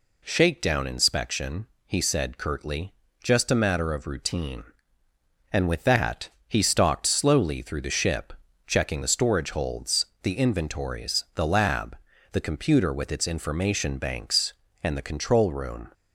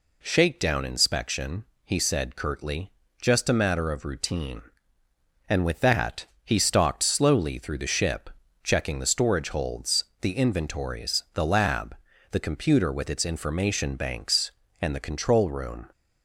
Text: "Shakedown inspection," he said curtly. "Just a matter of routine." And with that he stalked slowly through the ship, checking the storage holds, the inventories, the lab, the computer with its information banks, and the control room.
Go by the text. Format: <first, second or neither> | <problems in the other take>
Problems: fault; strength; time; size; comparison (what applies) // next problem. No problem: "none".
neither | pauses between "that" and "he"; slight; the same in both